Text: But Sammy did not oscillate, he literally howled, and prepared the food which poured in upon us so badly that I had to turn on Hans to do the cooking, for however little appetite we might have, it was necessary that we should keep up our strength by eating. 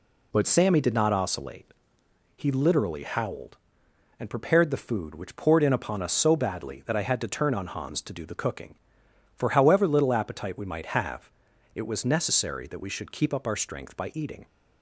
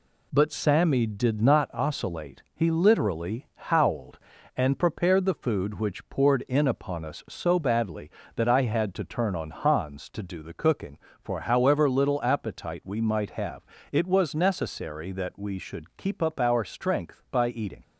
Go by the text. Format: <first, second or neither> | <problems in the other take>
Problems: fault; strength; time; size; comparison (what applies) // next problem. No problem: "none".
second | changes voice at "Sammy"; from 0.4 s on; 14.0 s long